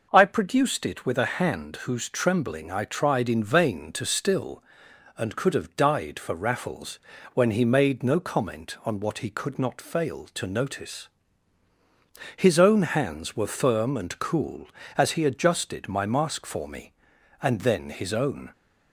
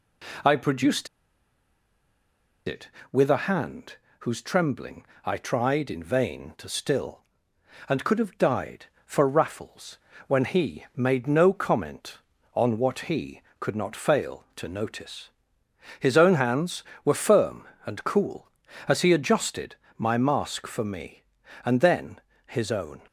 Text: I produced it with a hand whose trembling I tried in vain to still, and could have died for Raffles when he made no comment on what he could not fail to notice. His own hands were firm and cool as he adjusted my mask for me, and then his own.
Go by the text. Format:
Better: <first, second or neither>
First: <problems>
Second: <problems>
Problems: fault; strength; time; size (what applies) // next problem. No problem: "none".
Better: first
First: pauses between "Raffles" and "when"; slight; at 6.9 s; 0.34 s long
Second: pauses between "produced" and "it"; strong; at 1.0 s; 1.5 s long // pauses between "hand" and "whose"; slight; at 3.9 s; 0.24 s long // pauses between "trembling" and "I"; slight; at 5.0 s; 0.20 s long // pauses between "Raffles" and "when"; slight; at 9.9 s; 0.30 s long // pauses between "adjusted" and "my"; slight; at 19.7 s; 0.22 s long // pauses between "then" and "his"; slight; at 22.2 s; 0.24 s long